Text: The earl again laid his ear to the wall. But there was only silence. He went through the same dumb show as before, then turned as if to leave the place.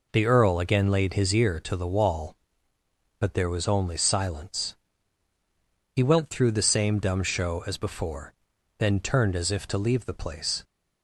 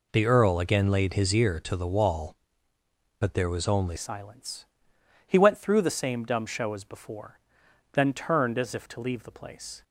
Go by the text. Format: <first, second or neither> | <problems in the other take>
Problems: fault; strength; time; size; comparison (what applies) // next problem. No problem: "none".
first | changes voice at "silence"; from 3.9 s on; 5.9 s long